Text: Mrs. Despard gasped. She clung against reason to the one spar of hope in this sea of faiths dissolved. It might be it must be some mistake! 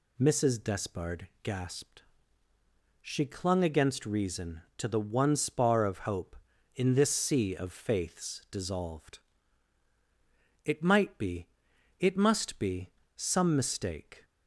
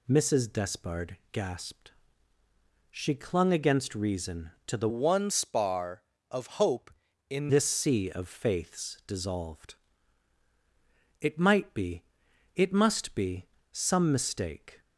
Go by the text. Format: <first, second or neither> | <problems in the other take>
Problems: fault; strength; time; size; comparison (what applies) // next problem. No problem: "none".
first | pauses between "Despard" and "gasped"; slight; at 1.1 s; 0.16 s long; slight in the first // changes voice from "one" to "in"; from 4.8 to 7.5 s; 2.7 s long // pauses between "be" and "it"; noticeable; at 12.0 s; 0.52 s long; noticeable in the first // pauses between "be" and "some"; slight; at 13.4 s; 0.26 s long; slight in the first